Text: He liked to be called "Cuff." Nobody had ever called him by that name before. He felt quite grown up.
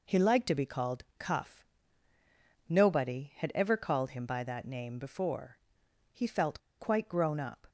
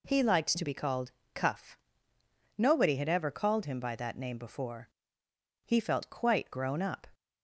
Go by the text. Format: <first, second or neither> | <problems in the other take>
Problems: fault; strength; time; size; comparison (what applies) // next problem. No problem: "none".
second | pauses between "called" and "Cuff"; slight; at 1.0 s; 0.16 s long; slight in the second // pauses between "felt" and "quite"; slight; at 6.5 s; 0.19 s long